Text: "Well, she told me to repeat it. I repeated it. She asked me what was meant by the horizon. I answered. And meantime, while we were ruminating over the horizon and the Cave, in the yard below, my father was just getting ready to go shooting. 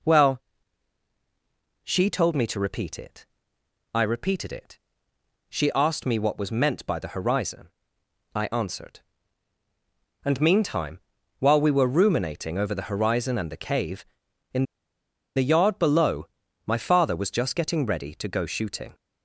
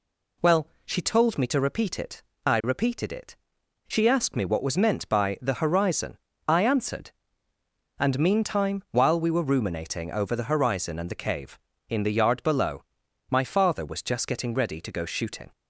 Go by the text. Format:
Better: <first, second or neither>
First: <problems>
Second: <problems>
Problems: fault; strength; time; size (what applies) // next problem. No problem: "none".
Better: second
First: pauses between "in" and "the"; noticeable; at 14.6 s; 0.72 s long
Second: none